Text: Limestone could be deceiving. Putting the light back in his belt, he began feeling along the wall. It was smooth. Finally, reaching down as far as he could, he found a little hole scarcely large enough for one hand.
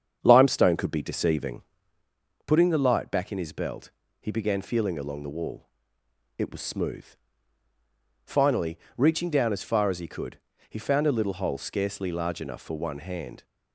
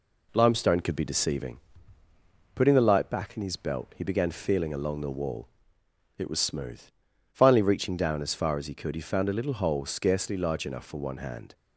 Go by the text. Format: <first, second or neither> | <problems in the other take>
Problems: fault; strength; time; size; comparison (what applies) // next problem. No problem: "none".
second | starts louder than the rest; strong; until 2.1 s; 7.5 dB